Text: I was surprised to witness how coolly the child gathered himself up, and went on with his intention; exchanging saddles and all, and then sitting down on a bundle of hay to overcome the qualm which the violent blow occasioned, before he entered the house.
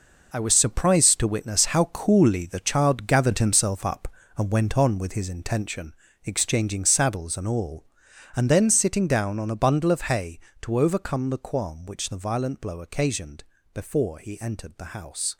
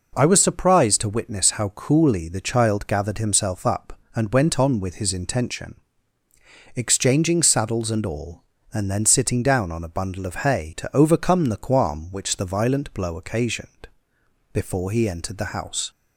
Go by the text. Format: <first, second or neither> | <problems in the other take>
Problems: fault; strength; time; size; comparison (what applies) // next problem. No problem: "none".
second | gets quieter; strong; throughout; 10.5 dB